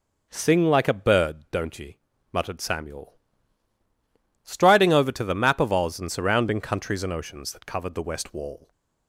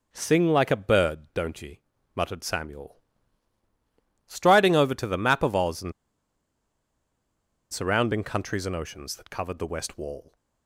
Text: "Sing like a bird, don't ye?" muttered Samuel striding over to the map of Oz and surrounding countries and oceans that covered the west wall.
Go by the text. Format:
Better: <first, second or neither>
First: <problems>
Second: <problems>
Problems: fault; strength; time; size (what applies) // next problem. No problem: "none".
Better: first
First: pauses between "Samuel" and "striding"; strong; at 3.1 s; 1.3 s long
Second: pauses between "Samuel" and "striding"; strong; at 2.9 s; 1.3 s long // pauses between "and" and "surrounding"; strong; at 5.9 s; 1.8 s long